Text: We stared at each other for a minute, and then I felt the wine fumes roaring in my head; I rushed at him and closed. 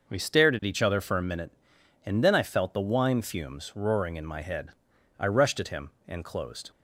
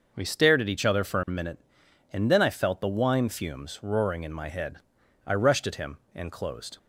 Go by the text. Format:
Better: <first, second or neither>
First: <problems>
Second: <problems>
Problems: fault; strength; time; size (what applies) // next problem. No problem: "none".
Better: neither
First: none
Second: none